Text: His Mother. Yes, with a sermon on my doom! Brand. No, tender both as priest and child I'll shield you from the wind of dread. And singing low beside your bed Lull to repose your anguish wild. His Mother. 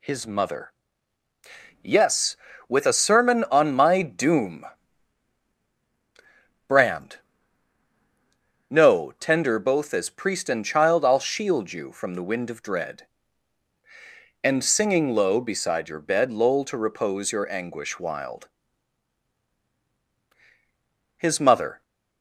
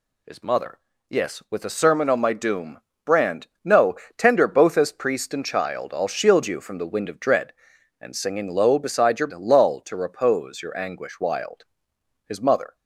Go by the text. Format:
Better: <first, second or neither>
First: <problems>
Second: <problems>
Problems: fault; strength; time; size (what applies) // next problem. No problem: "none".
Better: first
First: none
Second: skips "bed"; at 9.3 s